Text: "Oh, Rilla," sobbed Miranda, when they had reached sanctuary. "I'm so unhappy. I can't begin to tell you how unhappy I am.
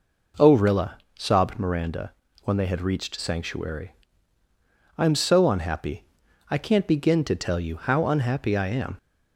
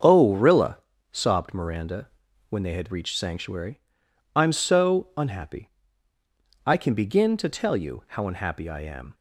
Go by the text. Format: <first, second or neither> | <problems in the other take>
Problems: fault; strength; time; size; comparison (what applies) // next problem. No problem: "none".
first | starts louder than the rest; until 1.3 s; 6.5 dB // says "can" for "can't"; at 6.7 s